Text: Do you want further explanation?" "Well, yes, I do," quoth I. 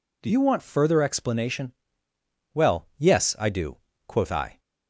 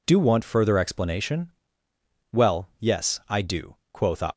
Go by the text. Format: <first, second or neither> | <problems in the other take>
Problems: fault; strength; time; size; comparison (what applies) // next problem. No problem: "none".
first | skips "you"; at 0.1 s